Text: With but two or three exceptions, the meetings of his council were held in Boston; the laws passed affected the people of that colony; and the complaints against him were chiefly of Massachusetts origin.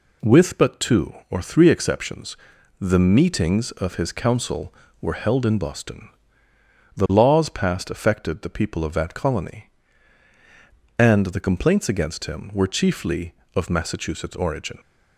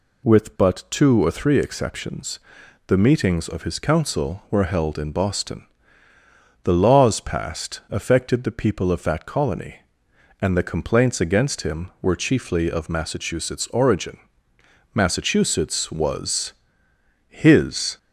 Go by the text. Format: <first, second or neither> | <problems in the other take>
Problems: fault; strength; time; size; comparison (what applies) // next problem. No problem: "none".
first | goes on to say "Massachusetts was his"; strong; from 14.9 s on; 3.0 s long